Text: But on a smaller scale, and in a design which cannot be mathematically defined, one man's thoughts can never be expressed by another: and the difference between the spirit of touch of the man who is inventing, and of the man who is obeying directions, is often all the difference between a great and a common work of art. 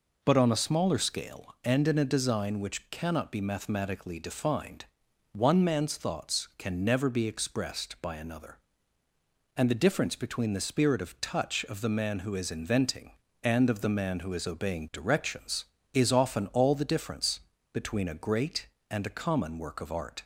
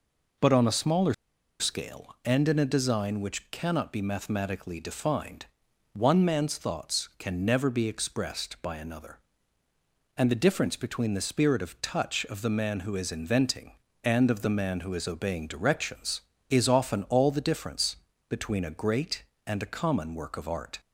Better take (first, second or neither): first